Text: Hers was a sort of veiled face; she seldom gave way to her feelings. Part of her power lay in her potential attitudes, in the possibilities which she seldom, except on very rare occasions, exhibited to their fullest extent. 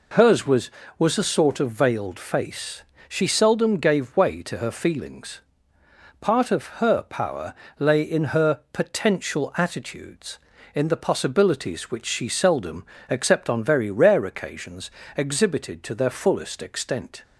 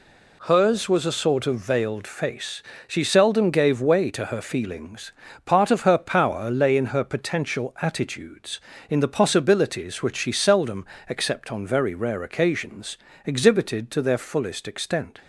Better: second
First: says "was" twice; at 0.9 s // pauses between "of" and "her"; slight; at 6.6 s; 0.16 s long // pauses between "power" and "lay"; slight; at 7.5 s; 0.24 s long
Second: none

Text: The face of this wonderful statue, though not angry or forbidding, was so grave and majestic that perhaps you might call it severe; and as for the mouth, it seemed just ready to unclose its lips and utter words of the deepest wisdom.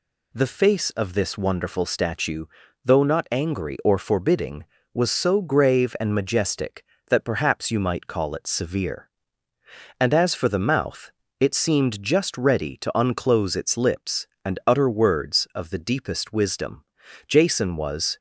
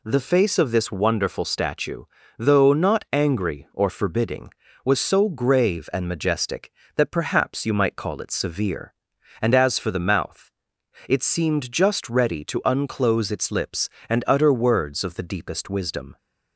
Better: second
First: goes on to say "Jason was"; noticeable; from 17.2 s on; 0.90 s long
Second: none

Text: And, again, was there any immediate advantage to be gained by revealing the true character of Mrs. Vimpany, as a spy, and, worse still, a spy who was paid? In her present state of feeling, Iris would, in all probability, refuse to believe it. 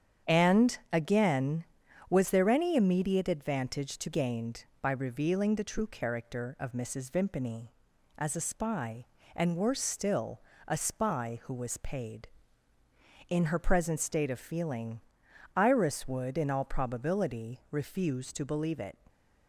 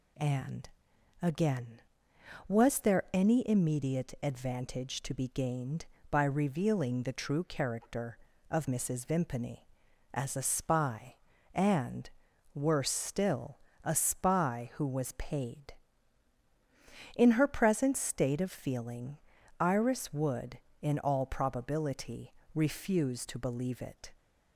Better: second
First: starts louder than the rest; strong; until 1.4 s; 8.5 dB // skips "be"; at 4.1 s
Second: none

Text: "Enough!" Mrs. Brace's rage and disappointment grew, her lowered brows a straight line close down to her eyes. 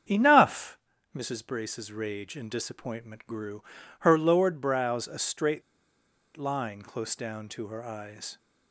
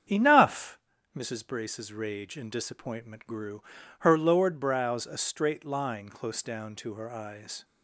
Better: second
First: starts louder than the rest; strong; until 1.4 s; 7.5 dB // pauses between "straight" and "line"; noticeable; at 5.6 s; 0.75 s long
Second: starts louder than the rest; strong; until 1.4 s; 8 dB

